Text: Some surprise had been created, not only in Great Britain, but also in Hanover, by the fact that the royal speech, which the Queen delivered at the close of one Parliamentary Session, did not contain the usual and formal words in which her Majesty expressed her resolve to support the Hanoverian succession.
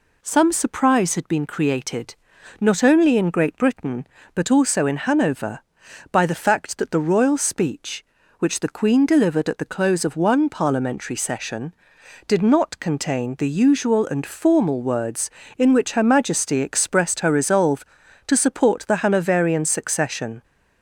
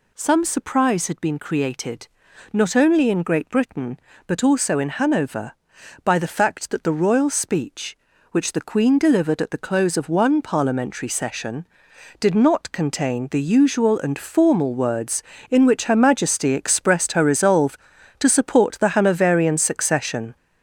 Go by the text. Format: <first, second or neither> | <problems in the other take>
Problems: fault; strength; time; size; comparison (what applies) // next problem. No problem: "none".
first | gets louder; throughout; 6 dB